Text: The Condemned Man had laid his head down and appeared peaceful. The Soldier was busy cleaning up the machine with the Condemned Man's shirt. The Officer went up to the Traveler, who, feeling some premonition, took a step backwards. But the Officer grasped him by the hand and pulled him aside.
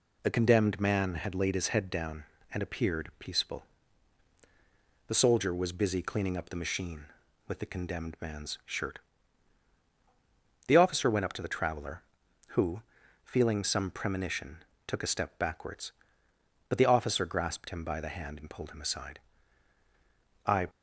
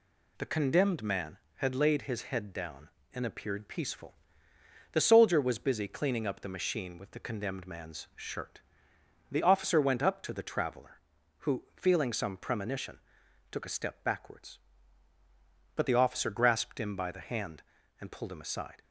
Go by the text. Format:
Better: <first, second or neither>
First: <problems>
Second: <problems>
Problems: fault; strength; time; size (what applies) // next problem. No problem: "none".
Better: second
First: goes on to say "I"; slight; from 20.4 s on; 0.22 s long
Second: none